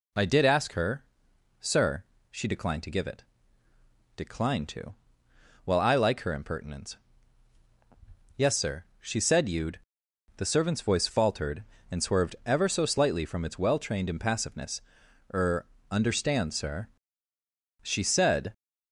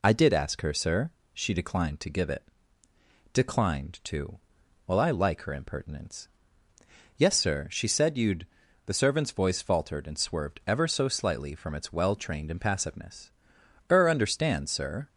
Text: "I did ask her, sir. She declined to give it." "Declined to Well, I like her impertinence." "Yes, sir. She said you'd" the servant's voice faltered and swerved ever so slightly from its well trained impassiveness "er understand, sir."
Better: second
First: pauses between "to" and "Well"; noticeable; at 4.9 s; 0.70 s long // pauses between "you'd" and "the"; noticeable; at 9.7 s; 0.58 s long // pauses between "impassiveness" and "er"; noticeable; at 14.8 s; 0.50 s long // pauses between "er" and "understand"; slight; at 15.6 s; 0.26 s long // goes on to say "She said"; noticeable; from 17.8 s on; 0.72 s long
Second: pauses between "to" and "Well"; noticeable; at 4.3 s; 0.48 s long // pauses between "you'd" and "the"; at 8.4 s; 0.40 s long // pauses between "impassiveness" and "er"; noticeable; at 13.3 s; 0.58 s long

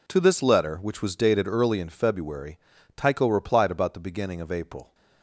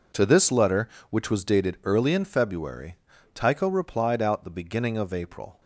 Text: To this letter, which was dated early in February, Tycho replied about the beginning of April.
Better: first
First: none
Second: says "out" for "about"; at 4.2 s

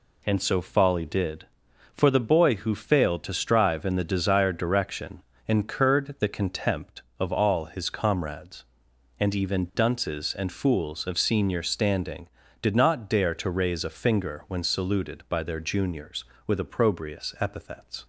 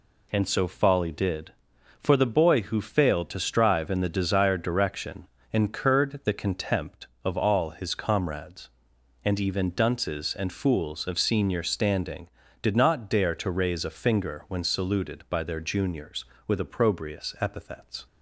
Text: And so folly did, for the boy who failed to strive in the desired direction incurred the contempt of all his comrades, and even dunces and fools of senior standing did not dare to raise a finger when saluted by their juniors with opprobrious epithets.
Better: neither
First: pauses between "direction" and "incurred"; slight; at 5.2 s; 0.26 s long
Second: pauses between "direction" and "incurred"; slight; at 5.2 s; 0.26 s long

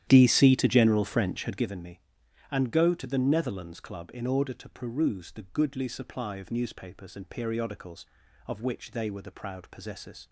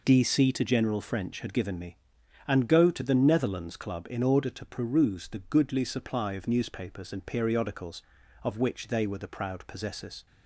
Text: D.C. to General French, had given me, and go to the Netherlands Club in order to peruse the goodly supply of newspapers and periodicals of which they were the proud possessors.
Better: second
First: starts louder than the rest; strong; until 1.7 s; 11 dB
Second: none

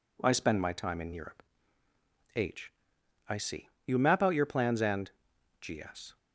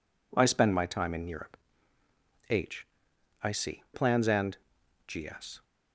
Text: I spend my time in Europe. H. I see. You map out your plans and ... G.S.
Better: first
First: none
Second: skips "You map out your"; at 3.8 s

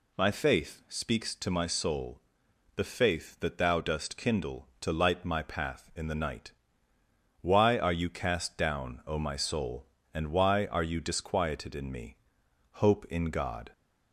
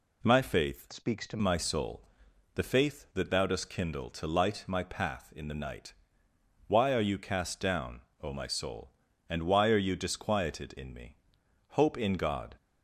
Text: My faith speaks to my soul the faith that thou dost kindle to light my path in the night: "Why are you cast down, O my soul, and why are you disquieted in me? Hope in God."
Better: first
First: pauses between "soul" and "the"; noticeable; at 2.1 s; 0.56 s long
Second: changes voice from "speaks" to "to"; from 0.9 to 1.3 s; 0.4 s long // pauses between "soul" and "the"; noticeable; at 2.0 s; 0.54 s long

